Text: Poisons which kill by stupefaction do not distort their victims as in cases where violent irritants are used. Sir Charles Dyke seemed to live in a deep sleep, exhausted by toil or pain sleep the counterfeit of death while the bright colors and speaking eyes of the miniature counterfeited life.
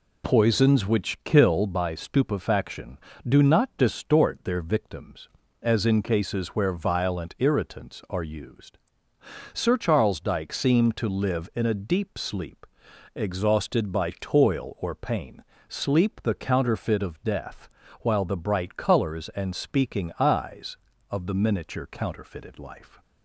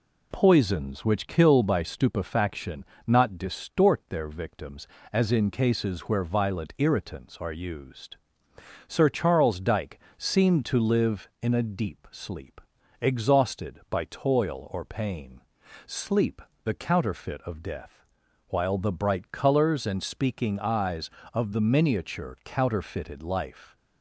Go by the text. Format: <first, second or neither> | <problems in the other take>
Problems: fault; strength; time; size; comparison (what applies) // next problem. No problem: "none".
first | skips "do"; at 2.9 s // pauses between "Dyke" and "seemed"; slight; at 9.9 s; 0.18 s long // pauses between "pain" and "sleep"; noticeable; at 15.4 s; 0.46 s long; slight in the first // pauses between "sleep" and "the"; slight; at 16.4 s; 0.24 s long // pauses between "death" and "while"; noticeable; at 18.0 s; 0.46 s long; slight in the first